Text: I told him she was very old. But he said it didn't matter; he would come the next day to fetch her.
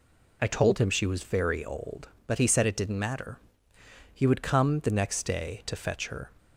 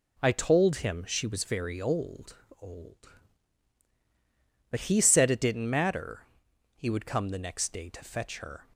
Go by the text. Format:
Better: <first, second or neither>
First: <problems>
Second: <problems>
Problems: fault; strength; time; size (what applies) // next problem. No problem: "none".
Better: first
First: none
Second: says "old" twice; at 2.5 s